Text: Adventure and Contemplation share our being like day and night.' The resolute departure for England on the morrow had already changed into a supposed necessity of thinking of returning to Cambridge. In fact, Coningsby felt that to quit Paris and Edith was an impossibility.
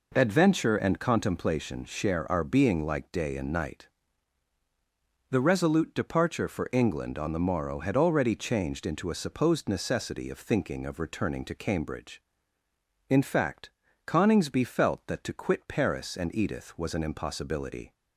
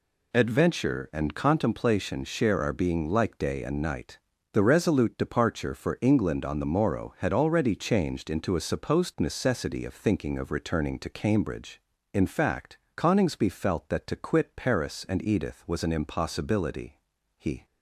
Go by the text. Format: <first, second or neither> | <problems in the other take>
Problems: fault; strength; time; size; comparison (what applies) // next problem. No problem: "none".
first | goes on to say "He"; slight; from 17.3 s on; 0.26 s long